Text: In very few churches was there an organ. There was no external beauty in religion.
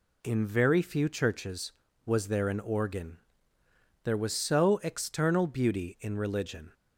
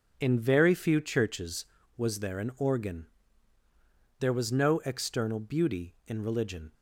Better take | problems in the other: second | says "so" for "no"; at 4.3 s

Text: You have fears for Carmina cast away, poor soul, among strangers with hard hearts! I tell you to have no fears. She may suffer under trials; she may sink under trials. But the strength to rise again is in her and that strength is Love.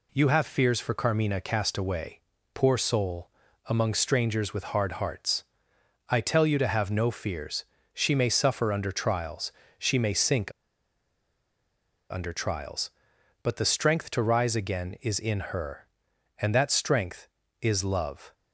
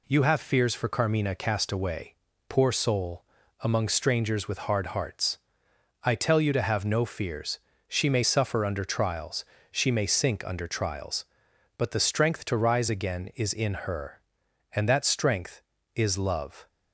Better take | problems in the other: second | pauses between "sink" and "under"; strong; at 10.5 s; 1.5 s long

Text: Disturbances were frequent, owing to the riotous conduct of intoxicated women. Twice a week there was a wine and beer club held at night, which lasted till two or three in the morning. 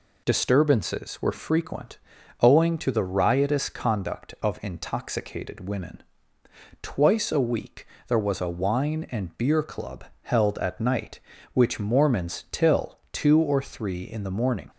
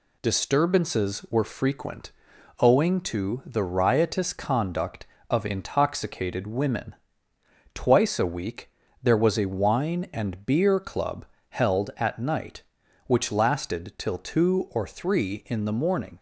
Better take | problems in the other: second | pauses between "week" and "there"; slight; at 7.8 s; 0.22 s long; slight in the second // pauses between "club" and "held"; slight; at 10.0 s; 0.20 s long; slight in the second // says "mormons" for "lasted"; at 11.7 s

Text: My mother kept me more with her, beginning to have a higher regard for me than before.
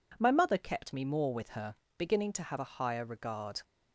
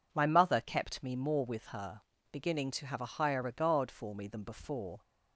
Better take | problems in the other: second | stops before "for me than before"; at 3.6 s

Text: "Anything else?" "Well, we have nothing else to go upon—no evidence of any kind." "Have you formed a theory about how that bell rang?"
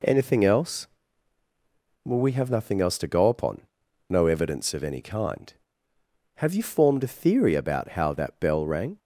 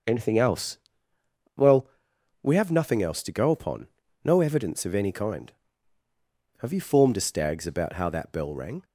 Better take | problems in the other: first | starts louder than the rest; noticeable; until 1.8 s; 6 dB // says "stags" for "theory"; at 7.2 s

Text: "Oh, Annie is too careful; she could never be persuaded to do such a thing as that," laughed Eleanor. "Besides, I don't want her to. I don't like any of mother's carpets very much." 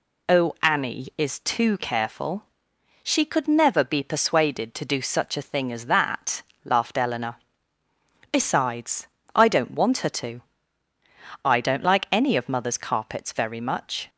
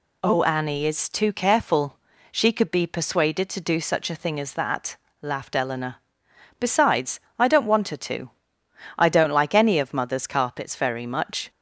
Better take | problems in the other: first | skips "never"; at 2.7 s

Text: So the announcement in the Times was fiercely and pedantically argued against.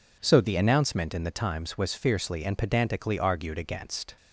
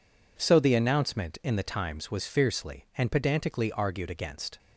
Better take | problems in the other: neither | none

